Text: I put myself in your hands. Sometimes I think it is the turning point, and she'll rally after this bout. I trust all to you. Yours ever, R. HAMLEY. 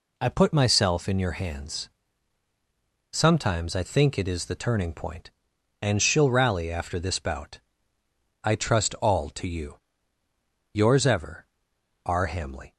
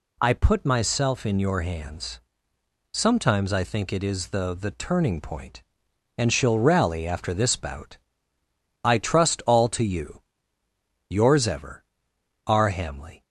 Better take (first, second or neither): first